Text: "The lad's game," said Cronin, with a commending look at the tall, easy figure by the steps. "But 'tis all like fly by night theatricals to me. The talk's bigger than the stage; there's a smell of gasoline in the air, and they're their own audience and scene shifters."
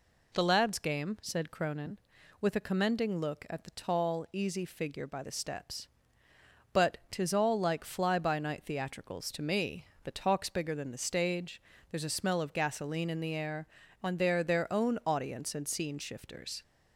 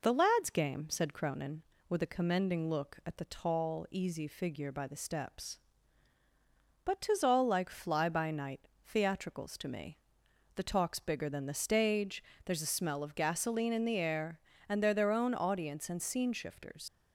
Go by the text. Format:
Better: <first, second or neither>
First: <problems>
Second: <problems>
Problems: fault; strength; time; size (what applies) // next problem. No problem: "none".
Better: first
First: none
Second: pauses between "night" and "theatricals"; slight; at 8.6 s; 0.16 s long // leaves "shifters" unfinished; at 16.8 s; 85 ms